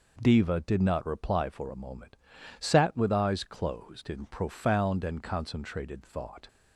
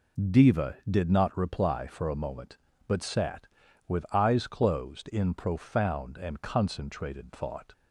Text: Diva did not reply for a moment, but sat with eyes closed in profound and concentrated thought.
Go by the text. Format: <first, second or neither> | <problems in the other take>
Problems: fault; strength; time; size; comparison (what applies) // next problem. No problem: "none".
second | skips "but"; at 2.3 s